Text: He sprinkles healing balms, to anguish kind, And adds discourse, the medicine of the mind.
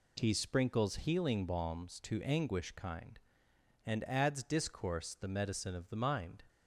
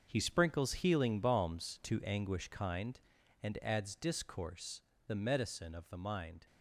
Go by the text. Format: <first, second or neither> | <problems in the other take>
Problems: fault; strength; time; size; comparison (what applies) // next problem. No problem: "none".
first | gets quieter; strong; throughout; 11.5 dB